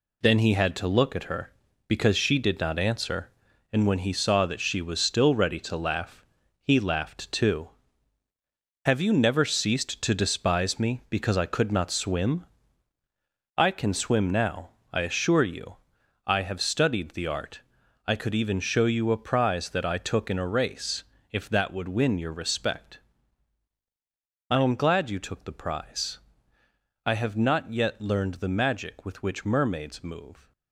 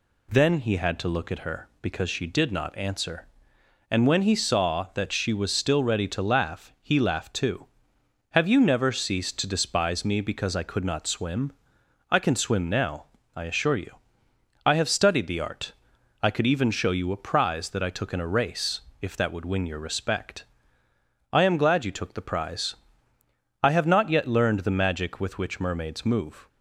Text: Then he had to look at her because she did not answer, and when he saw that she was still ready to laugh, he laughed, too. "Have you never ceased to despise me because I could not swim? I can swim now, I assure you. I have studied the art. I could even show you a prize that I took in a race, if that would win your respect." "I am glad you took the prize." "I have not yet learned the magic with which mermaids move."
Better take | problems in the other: second | gets quieter; strong; throughout; 8 dB

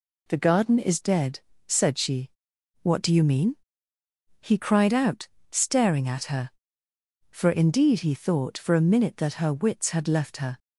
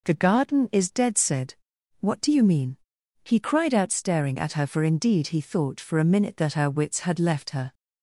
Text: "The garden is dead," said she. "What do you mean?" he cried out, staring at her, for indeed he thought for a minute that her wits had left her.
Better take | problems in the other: first | skips "she"; at 1.7 s

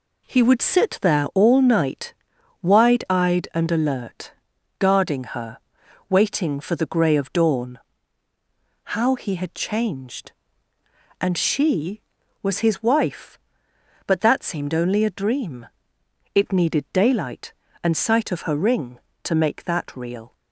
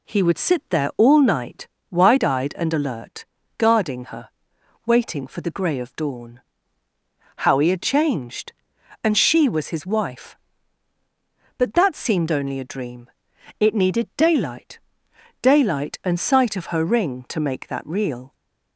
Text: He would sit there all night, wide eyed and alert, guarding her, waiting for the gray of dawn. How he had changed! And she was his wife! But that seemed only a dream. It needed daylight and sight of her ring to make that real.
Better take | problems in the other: first | says "daylight" twice; at 15.4 s

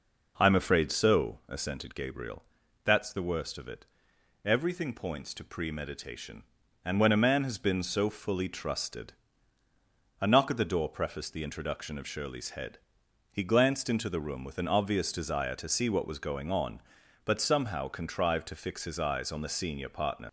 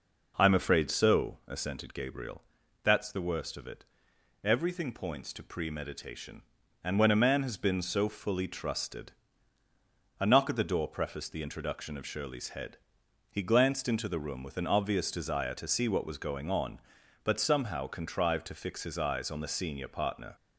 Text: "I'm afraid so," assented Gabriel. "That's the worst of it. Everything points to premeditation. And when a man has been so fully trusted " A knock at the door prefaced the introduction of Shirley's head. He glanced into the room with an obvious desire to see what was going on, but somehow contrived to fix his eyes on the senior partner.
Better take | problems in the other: second | starts louder than the rest; until 1.3 s; 6.5 dB; also in the second // leaves "partner" unfinished; at 20.2 s; 70 ms

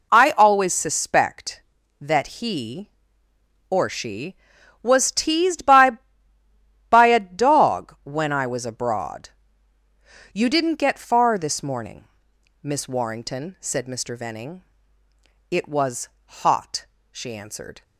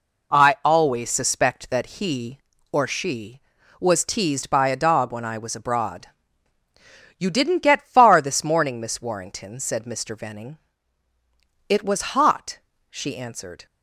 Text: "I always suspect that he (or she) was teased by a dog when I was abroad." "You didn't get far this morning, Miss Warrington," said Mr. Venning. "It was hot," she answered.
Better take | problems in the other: second | says "by" twice; at 6.8 s // pauses between "was" and "hot"; slight; at 16.0 s; 0.16 s long

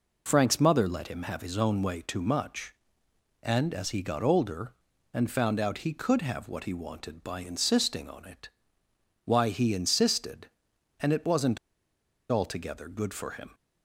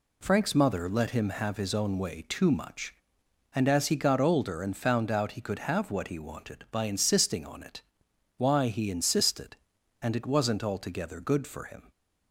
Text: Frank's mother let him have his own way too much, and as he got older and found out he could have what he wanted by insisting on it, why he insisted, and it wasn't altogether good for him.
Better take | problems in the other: second | pauses between "wasn't" and "altogether"; noticeable; at 11.5 s; 0.74 s long

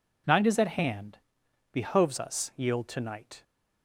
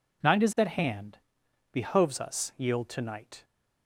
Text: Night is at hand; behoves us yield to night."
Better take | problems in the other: neither | none

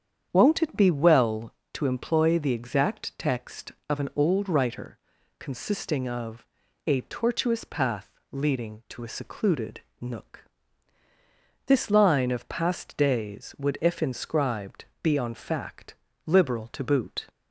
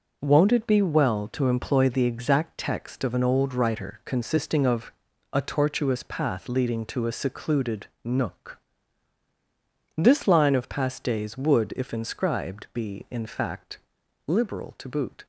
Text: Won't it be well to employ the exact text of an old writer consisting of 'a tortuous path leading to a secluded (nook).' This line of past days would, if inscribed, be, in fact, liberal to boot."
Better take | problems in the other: second | starts louder than the rest; strong; until 1.3 s; 8.5 dB // pauses between "writer" and "consisting"; at 4.9 s; 0.44 s long // pauses between "of" and "a"; at 6.4 s; 0.40 s long; also in the second // pauses between "path" and "leading"; slight; at 8.1 s; 0.18 s long // says "on" for "in"; at 15.1 s

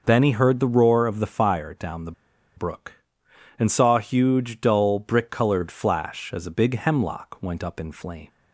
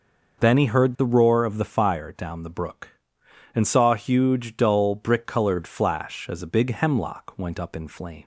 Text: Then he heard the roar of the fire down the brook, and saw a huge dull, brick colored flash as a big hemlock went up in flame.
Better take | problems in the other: second | pauses between "the" and "brook"; at 2.1 s; 0.45 s long

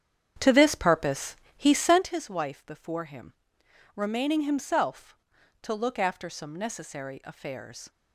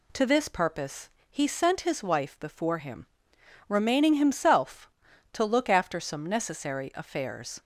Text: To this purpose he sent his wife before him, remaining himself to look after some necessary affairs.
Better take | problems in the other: second | starts louder than the rest; strong; until 2.1 s; 8.5 dB // pauses between "purpose" and "he"; slight; at 1.3 s; 0.20 s long; slight in the second

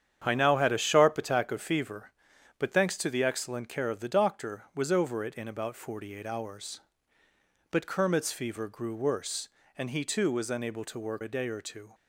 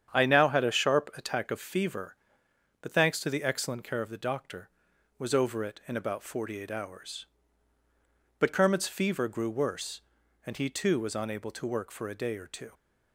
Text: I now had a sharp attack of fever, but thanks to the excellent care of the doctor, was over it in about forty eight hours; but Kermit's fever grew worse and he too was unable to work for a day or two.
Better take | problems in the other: second | starts louder than the rest; strong; until 1.2 s; 9 dB; strong in the second // skips "for"; at 11.2 s

